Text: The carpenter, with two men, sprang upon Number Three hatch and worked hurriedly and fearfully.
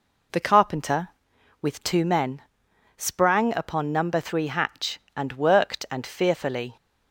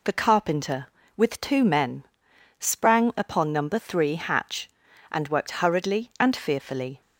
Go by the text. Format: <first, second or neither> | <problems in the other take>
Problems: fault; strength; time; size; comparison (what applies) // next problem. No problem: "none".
second | skips "hurriedly"; at 5.8 s